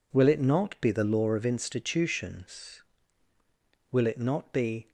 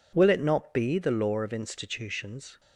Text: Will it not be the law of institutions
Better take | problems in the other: second | goes on to say "Will it not be"; noticeable; from 3.9 s on; 0.98 s long

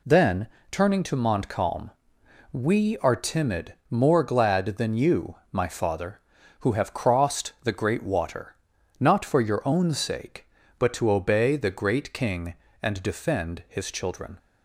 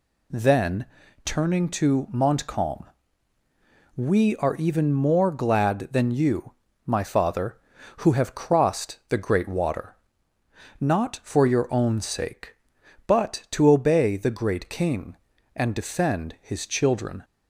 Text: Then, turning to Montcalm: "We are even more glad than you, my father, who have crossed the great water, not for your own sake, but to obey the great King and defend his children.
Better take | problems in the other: second | says "timid" for "even"; at 3.1 s

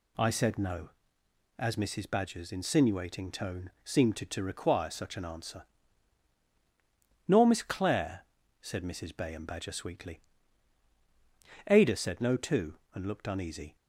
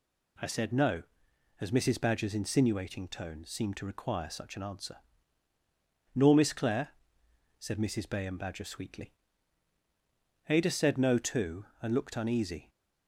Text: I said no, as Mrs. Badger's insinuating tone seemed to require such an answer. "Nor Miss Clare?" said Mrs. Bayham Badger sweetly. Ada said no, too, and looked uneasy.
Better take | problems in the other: second | says "to" twice; at 4.2 s

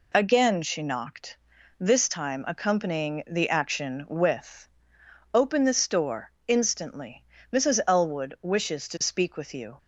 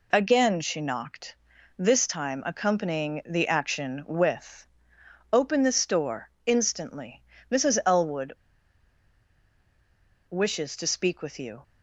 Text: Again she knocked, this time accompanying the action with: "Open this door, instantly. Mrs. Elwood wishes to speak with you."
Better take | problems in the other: first | pauses between "Elwood" and "wishes"; strong; at 8.3 s; 1.9 s long

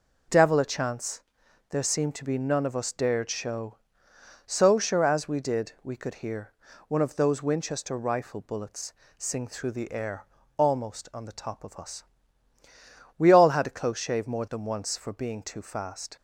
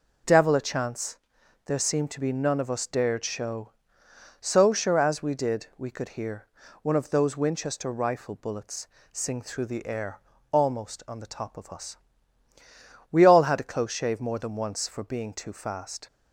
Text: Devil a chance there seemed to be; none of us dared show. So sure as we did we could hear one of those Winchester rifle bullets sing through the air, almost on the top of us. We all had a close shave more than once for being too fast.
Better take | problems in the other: neither | pauses between "chance" and "there"; noticeable; the same in both // pauses between "hear" and "one"; slight; the same in both // pauses between "bullets" and "sing"; slight; the same in both

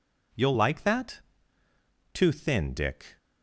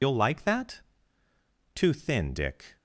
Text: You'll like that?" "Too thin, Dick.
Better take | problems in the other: first | loses the start of "You'll"; at 0.0 s; 85 ms

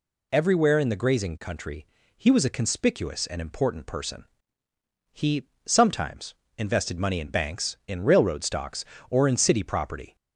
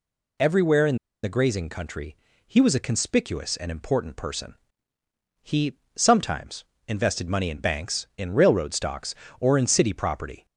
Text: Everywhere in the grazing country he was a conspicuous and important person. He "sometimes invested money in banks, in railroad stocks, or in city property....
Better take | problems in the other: first | pauses between "in" and "the"; slight; at 0.9 s; 0.27 s long // pauses between "country" and "he"; slight; at 2.1 s; 0.28 s long; slight in the first // pauses between "He" and "sometimes"; slight; at 5.7 s; 0.18 s long; slight in the first // pauses between "sometimes" and "invested"; slight; at 6.6 s; 0.22 s long; slight in the first

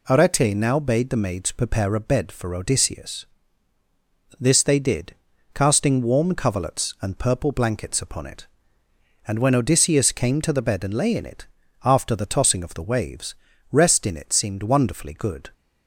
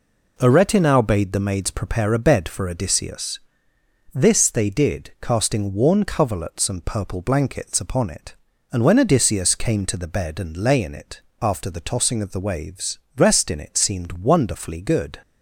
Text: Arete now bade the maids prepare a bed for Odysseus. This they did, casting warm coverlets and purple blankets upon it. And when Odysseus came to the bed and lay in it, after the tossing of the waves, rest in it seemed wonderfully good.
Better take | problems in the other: first | says "worn" for "warm"; at 5.7 s

